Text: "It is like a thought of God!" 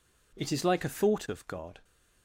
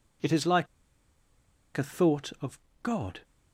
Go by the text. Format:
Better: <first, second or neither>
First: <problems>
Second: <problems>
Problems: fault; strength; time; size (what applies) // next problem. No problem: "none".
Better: first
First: none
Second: pauses between "like" and "a"; at 0.6 s; 1.0 s long // pauses between "of" and "God"; slight; at 2.5 s; 0.22 s long